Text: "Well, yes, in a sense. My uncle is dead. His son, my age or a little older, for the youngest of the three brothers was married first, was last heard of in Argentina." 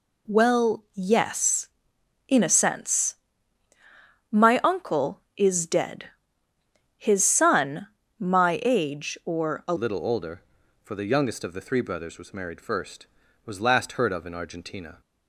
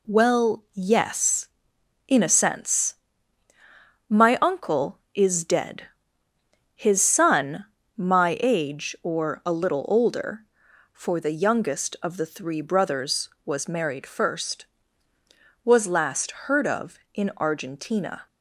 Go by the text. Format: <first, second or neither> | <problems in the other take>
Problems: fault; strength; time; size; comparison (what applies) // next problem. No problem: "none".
second | changes voice at "little"; from 9.7 s on; 5.3 s long